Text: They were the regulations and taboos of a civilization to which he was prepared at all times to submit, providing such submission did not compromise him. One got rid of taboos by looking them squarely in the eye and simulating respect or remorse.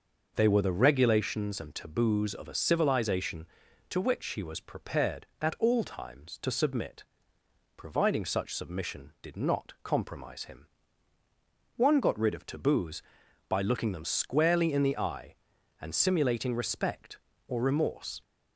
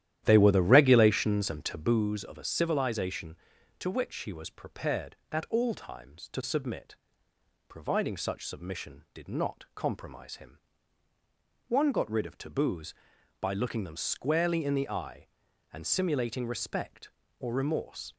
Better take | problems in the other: first | starts louder than the rest; strong; until 2.1 s; 12 dB

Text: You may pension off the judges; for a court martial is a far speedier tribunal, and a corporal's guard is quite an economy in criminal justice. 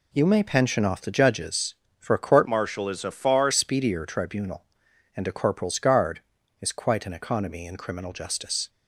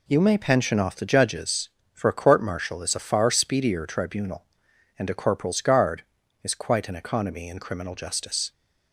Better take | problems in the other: second | changes voice from "martial" to "far"; from 2.4 to 3.5 s; 1.1 s long

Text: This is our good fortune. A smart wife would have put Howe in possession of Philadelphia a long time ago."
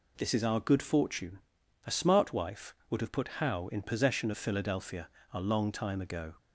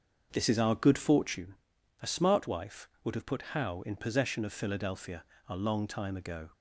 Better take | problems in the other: first | starts louder than the rest; until 1.4 s; 6.5 dB // pauses between "Philadelphia" and "a"; slight; at 5.2 s; 0.24 s long; slight in the first

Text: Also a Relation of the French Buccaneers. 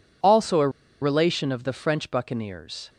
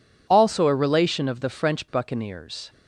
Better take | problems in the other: second | pauses between "a" and "Relation"; slight; at 0.6 s; 0.32 s long

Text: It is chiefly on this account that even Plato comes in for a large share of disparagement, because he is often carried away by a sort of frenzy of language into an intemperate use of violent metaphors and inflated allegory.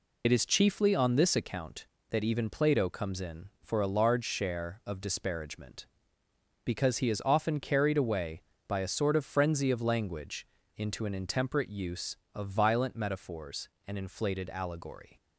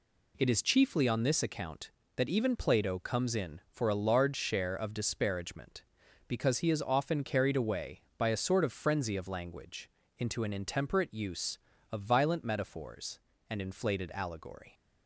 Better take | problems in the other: second | loses the start of "It"; at 0.2 s; 40 ms // pauses between "language" and "into"; slight; at 10.4 s; 0.30 s long; slight in the second

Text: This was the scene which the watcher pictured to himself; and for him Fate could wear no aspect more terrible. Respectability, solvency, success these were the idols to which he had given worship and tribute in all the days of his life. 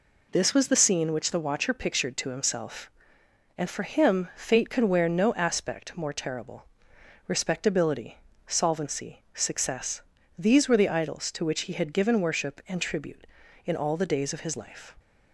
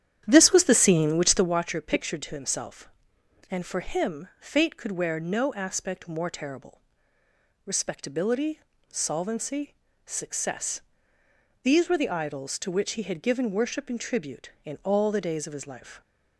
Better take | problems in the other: first | starts louder than the rest; strong; until 1.6 s; 10 dB // pauses between "success" and "these"; noticeable; at 10.7 s; 0.84 s long; slight in the first

